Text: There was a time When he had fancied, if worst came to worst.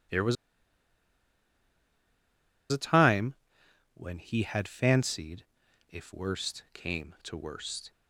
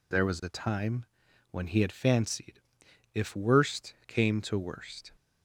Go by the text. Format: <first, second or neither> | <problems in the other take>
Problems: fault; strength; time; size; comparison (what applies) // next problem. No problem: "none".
second | pauses between "was" and "a"; strong; at 0.3 s; 2.3 s long // pauses between "time" and "When"; noticeable; at 3.3 s; 0.60 s long; also in the second